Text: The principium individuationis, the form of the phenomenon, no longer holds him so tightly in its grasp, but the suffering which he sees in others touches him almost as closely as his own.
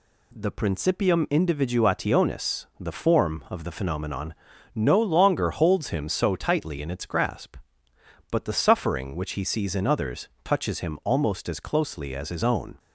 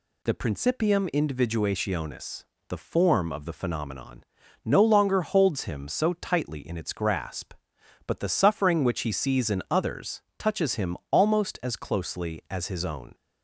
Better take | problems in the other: neither | pauses between "others" and "touches"; slight; the same in both

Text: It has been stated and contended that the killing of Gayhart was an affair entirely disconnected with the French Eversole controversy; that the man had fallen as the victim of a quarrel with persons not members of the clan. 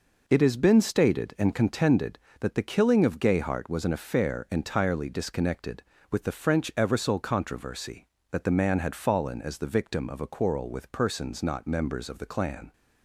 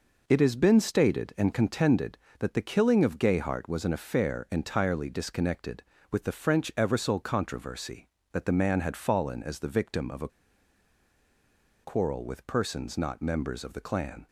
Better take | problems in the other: first | pauses between "a" and "quarrel"; strong; at 10.2 s; 1.5 s long

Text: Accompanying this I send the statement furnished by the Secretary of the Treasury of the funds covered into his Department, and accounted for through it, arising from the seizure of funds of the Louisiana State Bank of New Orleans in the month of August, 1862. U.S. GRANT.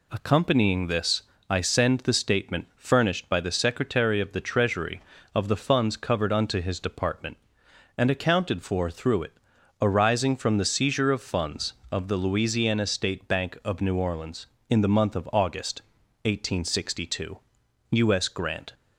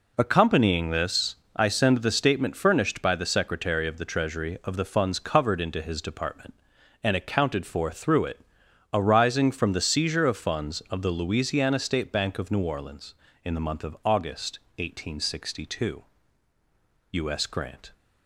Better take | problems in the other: second | pauses between "this" and "I"; slight; at 1.2 s; 0.26 s long; slight in the second // says "unto" for "into"; at 6.3 s

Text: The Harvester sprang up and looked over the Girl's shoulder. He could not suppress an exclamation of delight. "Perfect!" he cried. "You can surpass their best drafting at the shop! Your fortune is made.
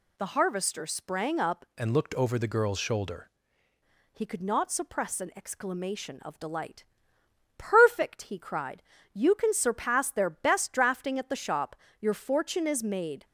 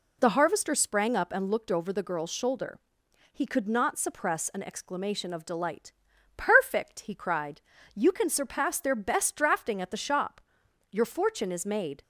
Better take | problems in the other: second | changes voice from "and" to "shoulder"; from 1.7 to 3.2 s; 1.5 s long

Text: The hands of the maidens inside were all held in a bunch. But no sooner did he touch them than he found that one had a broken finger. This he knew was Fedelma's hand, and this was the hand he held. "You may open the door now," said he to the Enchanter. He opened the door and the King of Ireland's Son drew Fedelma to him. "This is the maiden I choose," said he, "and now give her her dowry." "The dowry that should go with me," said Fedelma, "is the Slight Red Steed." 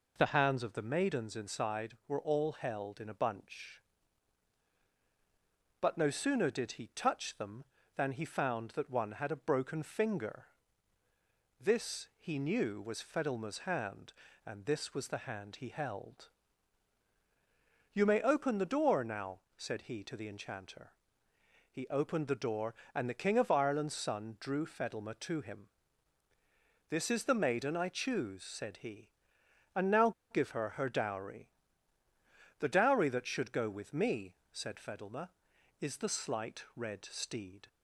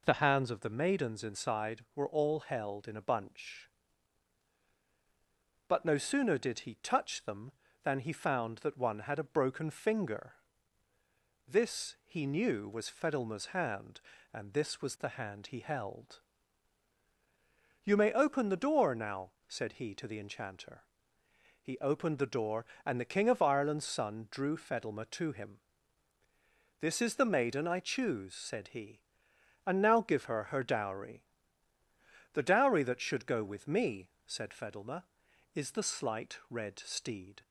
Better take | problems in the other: second | pauses between "now" and "give"; slight; at 30.1 s; 0.19 s long

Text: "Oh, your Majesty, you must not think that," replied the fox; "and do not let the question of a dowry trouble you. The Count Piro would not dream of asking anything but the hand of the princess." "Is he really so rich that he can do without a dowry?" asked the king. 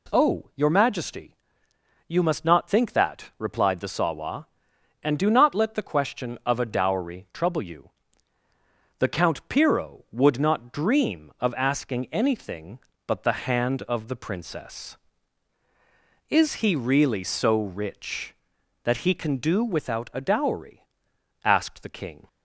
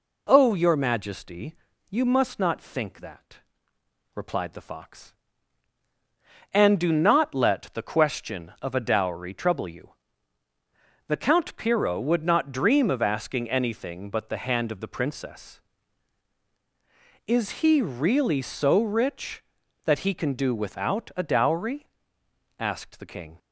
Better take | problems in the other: second | says "sawa" for "fox"; at 3.8 s

